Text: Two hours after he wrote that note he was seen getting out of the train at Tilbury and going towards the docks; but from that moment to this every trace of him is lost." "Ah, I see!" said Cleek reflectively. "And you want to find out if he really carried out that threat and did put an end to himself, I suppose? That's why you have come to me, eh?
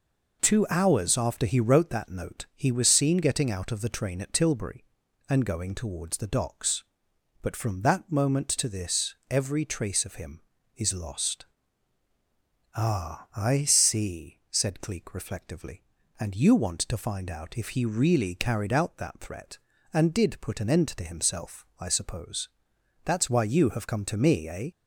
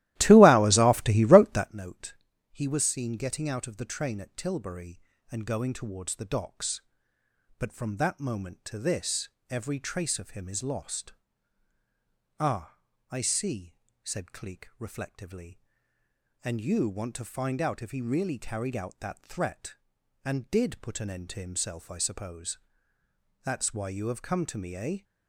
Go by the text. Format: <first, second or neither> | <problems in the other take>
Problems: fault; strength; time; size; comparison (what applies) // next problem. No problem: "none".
first | starts louder than the rest; strong; until 1.8 s; 16 dB // pauses between "note" and "he"; slight; at 2.1 s; 0.36 s long // pauses between "this" and "every"; slight; at 9.2 s; 0.20 s long